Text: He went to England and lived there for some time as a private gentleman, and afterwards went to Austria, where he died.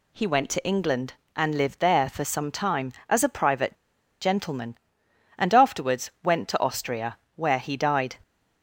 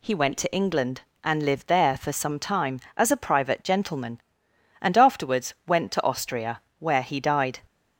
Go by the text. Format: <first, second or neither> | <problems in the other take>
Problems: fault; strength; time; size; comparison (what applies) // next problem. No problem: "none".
second | pauses between "private" and "gentleman"; noticeable; at 3.7 s; 0.47 s long